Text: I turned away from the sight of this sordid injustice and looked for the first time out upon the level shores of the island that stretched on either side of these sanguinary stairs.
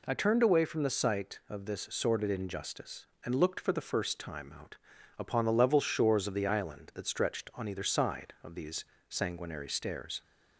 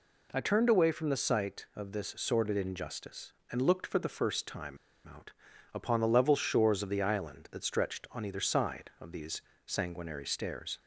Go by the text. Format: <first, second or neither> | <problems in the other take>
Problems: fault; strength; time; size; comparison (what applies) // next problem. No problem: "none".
first | pauses between "time" and "out"; slight; at 4.7 s; 0.29 s long // pauses between "out" and "upon"; at 5.3 s; 0.42 s long; also in the first // pauses between "these" and "sanguinary"; slight; at 9.4 s; 0.24 s long; slight in the first